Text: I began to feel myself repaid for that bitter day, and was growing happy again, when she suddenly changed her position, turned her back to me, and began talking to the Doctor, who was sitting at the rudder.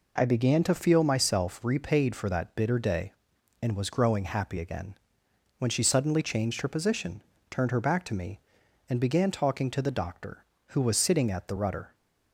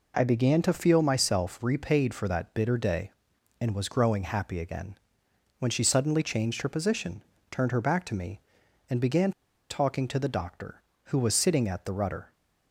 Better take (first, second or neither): first